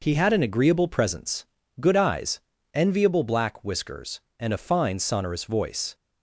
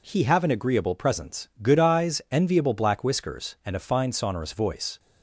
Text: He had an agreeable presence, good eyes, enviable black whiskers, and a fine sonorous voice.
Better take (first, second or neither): first